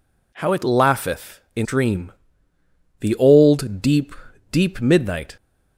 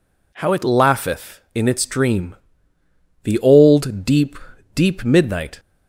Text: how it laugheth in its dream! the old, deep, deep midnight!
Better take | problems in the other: second | skips "its"; at 1.6 s

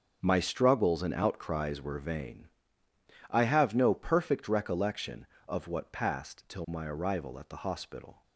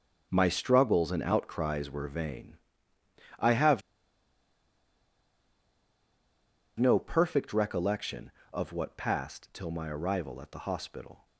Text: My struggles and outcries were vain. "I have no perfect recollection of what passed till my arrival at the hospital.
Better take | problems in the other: first | starts louder than the rest; until 1.3 s; 6.5 dB; also in the first // pauses between "have" and "no"; strong; at 3.8 s; 2.9 s long

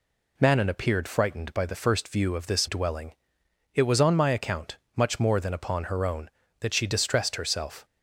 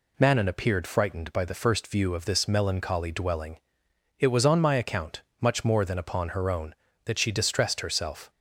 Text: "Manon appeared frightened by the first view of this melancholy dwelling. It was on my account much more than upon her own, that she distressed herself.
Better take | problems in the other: second | skips "melancholy"; at 2.6 s // pauses between "account" and "much"; slight; at 4.7 s; 0.18 s long; slight in the second

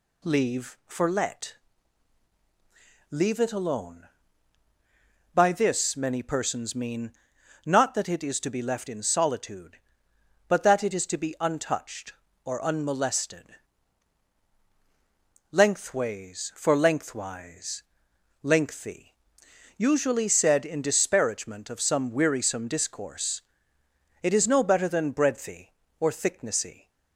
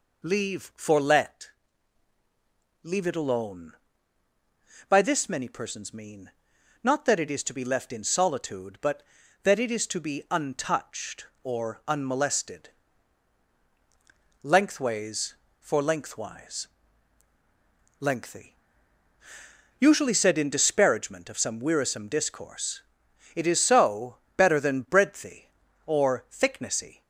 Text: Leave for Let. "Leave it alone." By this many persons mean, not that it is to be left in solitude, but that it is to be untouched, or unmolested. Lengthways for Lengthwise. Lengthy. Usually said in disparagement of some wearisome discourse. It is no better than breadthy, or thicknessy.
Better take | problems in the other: first | says "so" for "no"; at 23.5 s

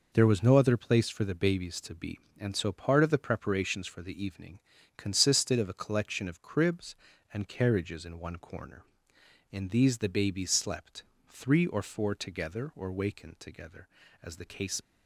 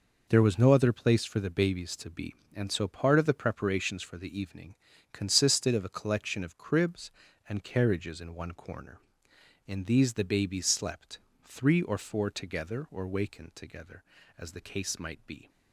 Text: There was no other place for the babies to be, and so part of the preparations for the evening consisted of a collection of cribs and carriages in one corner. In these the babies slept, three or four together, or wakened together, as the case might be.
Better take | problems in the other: second | pauses between "evening" and "consisted"; slight; at 4.5 s; 0.36 s long; slight in the second // stops before "might be"; at 14.8 s

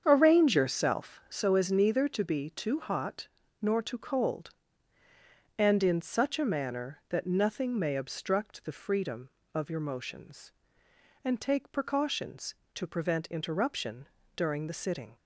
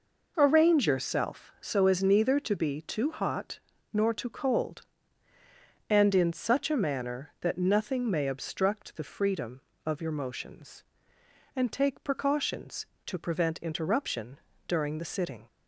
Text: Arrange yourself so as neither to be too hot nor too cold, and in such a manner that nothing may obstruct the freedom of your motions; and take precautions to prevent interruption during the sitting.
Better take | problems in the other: second | starts louder than the rest; strong; until 1.4 s; 7.5 dB // pauses between "hot" and "nor"; slight; at 3.2 s; 0.32 s long; slight in the second // pauses between "interruption" and "during"; slight; at 14.0 s; 0.30 s long; slight in the second

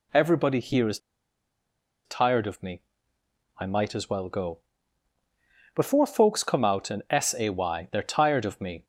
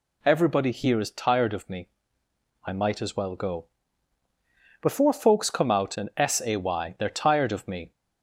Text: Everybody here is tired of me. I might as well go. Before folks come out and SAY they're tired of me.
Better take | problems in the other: second | pauses between "is" and "tired"; at 0.9 s; 1.0 s long

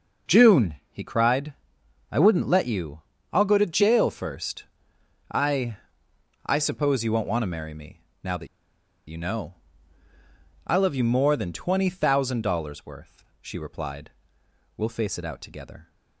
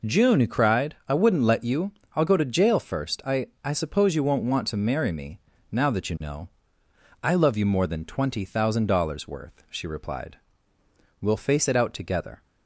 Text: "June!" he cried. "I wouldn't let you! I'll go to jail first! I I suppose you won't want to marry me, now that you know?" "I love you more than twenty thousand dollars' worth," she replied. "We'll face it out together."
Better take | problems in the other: second | pauses between "I" and "I"; noticeable; at 5.7 s; 0.68 s long; slight in the second // pauses between "that" and "you"; noticeable; at 8.4 s; 0.61 s long

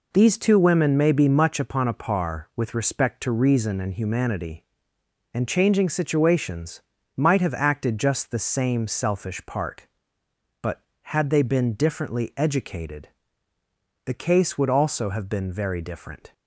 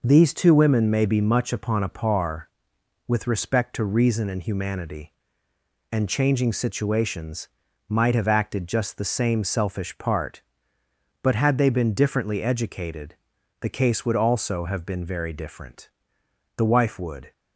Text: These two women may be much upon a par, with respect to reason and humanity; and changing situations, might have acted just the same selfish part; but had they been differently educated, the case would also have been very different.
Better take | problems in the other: first | goes on to say "The wife would"; noticeable; from 16.5 s on; 0.76 s long

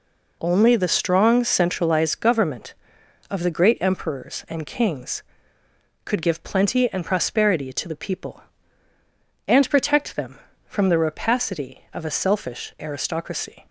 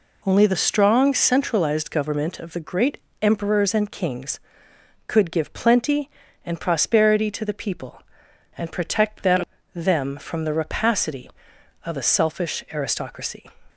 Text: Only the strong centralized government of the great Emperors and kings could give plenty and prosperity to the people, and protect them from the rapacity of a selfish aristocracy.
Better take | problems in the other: first | pauses between "great" and "Emperors"; slight; at 2.9 s; 0.22 s long // says "them" twice; at 9.7 s

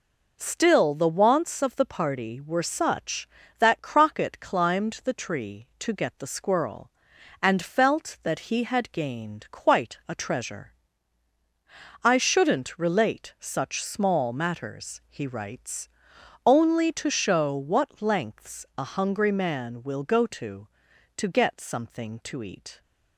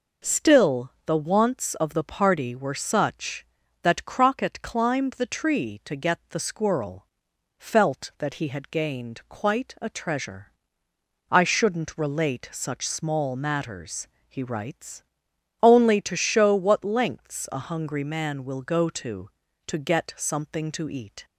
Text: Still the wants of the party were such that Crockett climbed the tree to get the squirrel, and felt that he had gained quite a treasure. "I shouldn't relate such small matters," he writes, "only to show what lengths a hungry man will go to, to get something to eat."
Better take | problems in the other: first | skips "and"; at 7.3 s

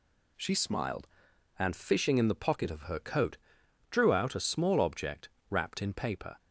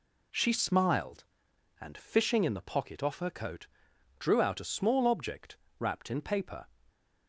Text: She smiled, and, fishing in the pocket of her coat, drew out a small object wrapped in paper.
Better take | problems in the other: first | says "off" for "of"; at 3.0 s // pauses between "object" and "wrapped"; slight; at 5.5 s; 0.24 s long; slight in the first

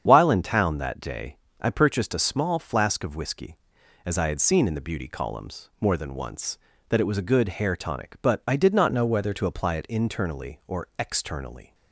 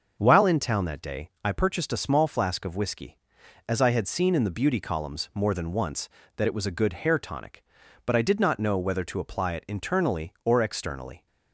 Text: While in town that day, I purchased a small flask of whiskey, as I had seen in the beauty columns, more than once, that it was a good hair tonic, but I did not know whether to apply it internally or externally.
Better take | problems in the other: second | starts louder than the rest; strong; until 1.0 s; 8 dB; also in the second // changes voice from "know" to "whether"; from 8.9 to 9.3 s; 0.4 s long

